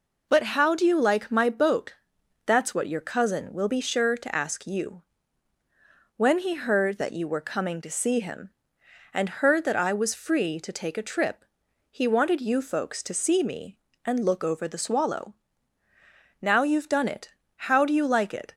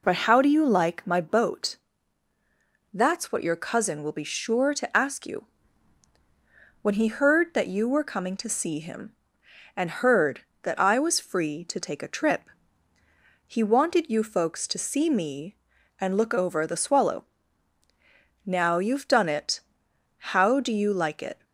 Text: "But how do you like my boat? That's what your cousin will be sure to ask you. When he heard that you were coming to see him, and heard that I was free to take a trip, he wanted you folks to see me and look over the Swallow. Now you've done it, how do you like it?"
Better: neither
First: none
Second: none

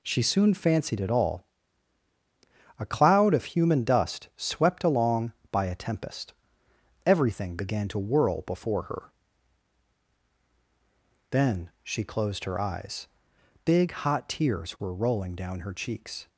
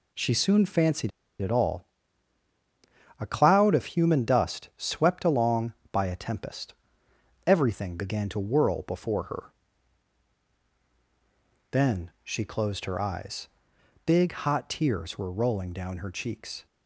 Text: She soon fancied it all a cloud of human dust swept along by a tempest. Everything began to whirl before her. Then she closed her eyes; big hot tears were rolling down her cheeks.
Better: first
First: pauses between "all" and "a"; strong; at 1.4 s; 1.3 s long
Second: pauses between "fancied" and "it"; slight; at 1.1 s; 0.30 s long // pauses between "all" and "a"; strong; at 1.8 s; 1.3 s long

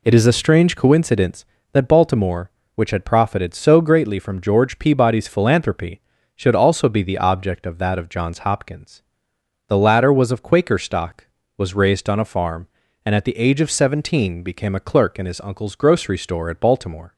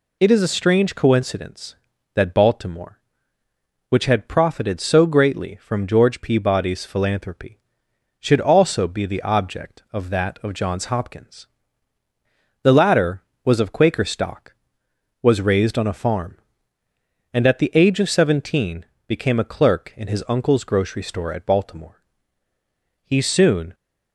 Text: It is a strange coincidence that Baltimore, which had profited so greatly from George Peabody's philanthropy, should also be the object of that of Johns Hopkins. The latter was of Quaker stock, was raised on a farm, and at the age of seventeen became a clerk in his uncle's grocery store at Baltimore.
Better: first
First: none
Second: pauses between "seventeen" and "became"; slight; at 18.8 s; 0.22 s long // goes on to say "He soon"; noticeable; from 23.0 s on; 0.70 s long

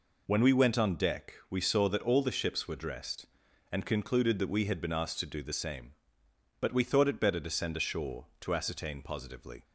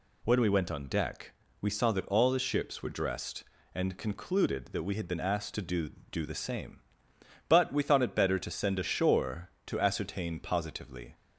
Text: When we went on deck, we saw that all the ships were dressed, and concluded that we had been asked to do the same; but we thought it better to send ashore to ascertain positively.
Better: first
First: none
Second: says "do" twice; at 6.1 s

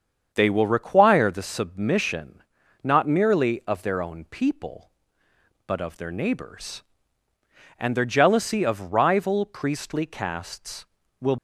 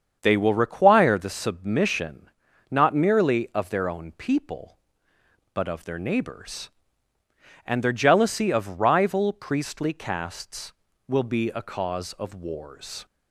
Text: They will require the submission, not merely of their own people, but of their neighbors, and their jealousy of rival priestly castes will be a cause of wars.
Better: second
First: starts louder than the rest; strong; until 1.3 s; 7 dB // stops before "be a cause of wars"; at 11.3 s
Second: starts louder than the rest; strong; until 1.2 s; 7 dB

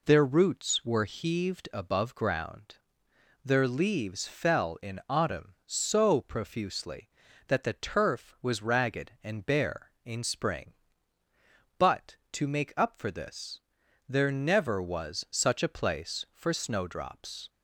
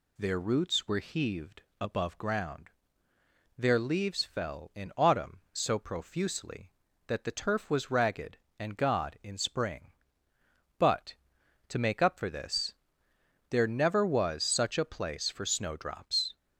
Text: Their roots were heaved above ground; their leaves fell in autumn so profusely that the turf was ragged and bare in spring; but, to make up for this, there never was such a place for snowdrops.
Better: first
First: none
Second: pauses between "heaved" and "above"; slight; at 1.6 s; 0.18 s long // says "god" for "bare"; at 8.7 s

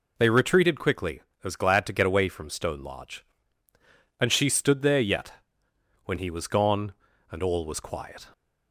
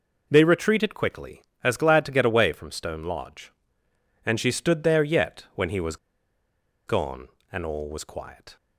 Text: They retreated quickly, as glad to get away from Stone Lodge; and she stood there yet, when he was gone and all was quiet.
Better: first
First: none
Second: pauses between "was" and "gone"; noticeable; at 5.9 s; 0.91 s long

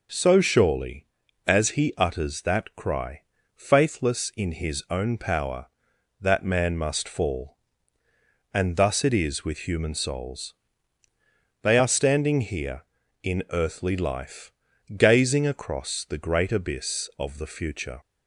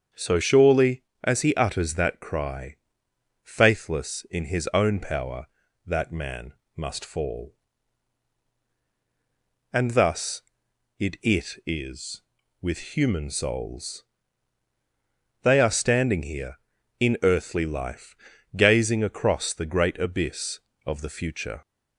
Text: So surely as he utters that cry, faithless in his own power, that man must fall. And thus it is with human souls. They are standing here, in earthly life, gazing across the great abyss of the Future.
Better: first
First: none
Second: starts louder than the rest; strong; until 1.3 s; 7 dB // pauses between "man" and "must"; slight; at 6.5 s; 0.24 s long // says "it" twice; at 11.2 s

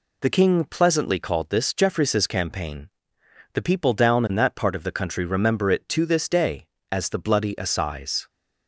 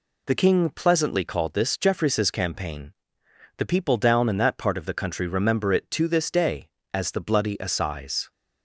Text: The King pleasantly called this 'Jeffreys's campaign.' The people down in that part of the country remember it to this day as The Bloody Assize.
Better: neither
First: none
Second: none

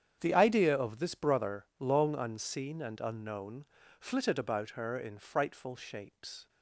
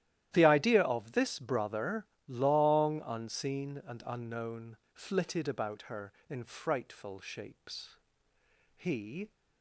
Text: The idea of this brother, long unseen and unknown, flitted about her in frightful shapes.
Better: first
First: starts louder than the rest; strong; until 1.2 s; 8.5 dB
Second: starts louder than the rest; strong; until 1.3 s; 12.5 dB // goes on to say "He"; from 8.7 s on; 0.54 s long

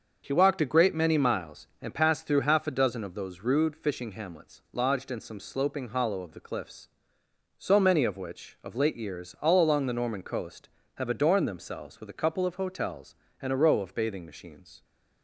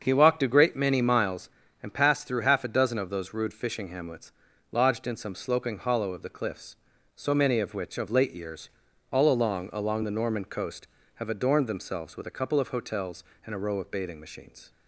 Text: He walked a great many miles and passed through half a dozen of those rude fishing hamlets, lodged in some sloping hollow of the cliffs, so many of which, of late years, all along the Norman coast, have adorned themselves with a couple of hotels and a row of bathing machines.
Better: first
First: starts louder than the rest; until 1.2 s; 6.5 dB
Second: starts louder than the rest; until 1.0 s; 7 dB // says "along" twice; at 9.7 s

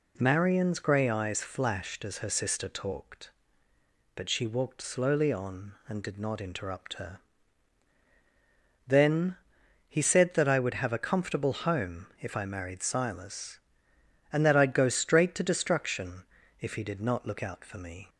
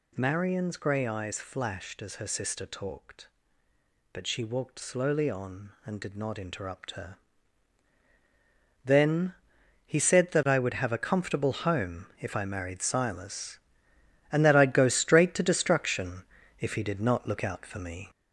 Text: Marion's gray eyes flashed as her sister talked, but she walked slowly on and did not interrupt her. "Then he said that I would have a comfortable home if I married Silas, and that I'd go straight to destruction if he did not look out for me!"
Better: first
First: pauses between "Then" and "he"; noticeable; at 9.3 s; 0.54 s long // pauses between "destruction" and "if"; at 16.2 s; 0.38 s long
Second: gets louder; noticeable; throughout; 5 dB // pauses between "Then" and "he"; noticeable; at 9.3 s; 0.54 s long // pauses between "destruction" and "if"; at 16.2 s; 0.38 s long

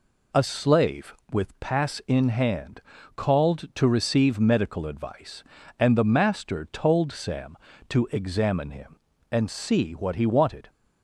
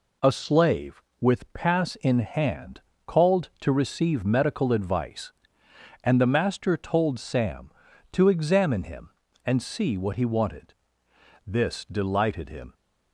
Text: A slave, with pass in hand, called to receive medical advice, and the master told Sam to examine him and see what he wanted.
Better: first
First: none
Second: goes on to say "This delighted him"; noticeable; from 11.4 s on; 1.2 s long

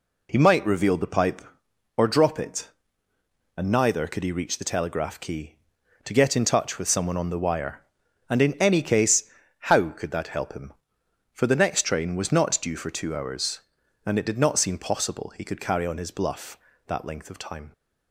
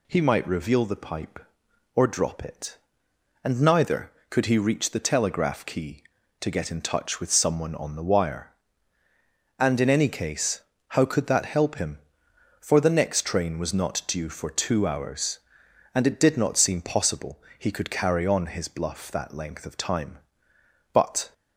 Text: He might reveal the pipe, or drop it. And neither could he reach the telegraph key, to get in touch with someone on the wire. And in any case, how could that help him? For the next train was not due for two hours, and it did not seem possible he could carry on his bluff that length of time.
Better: first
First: none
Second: pauses between "possible" and "he"; slight; at 17.4 s; 0.18 s long // goes on to say "But"; slight; from 20.9 s on; 0.40 s long

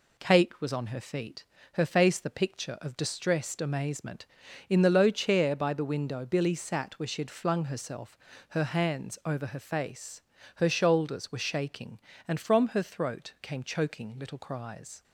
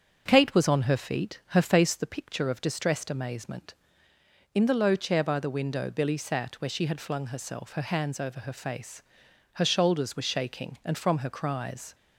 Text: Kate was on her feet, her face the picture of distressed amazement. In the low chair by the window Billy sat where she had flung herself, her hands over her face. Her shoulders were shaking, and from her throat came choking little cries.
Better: first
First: none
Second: starts louder than the rest; strong; until 1.2 s; 7.5 dB // skips "throat came choking little"; at 11.2 s

